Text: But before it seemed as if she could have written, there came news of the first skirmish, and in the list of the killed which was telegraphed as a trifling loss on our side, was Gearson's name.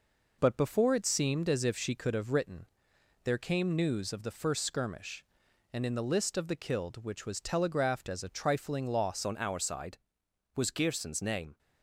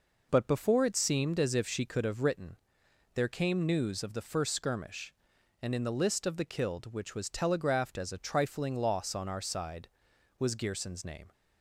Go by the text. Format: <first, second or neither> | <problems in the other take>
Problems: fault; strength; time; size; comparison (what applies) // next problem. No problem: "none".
second | changes voice at "on"; from 9.2 s on; 2.3 s long